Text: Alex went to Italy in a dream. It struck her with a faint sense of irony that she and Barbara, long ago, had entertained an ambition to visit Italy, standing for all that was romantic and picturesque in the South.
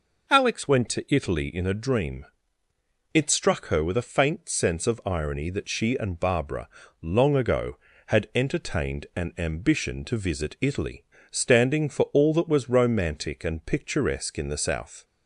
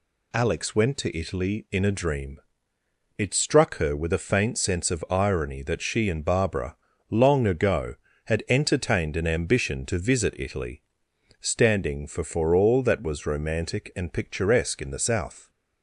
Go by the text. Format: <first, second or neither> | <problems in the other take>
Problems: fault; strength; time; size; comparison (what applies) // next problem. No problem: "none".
first | says "for" twice; at 12.2 s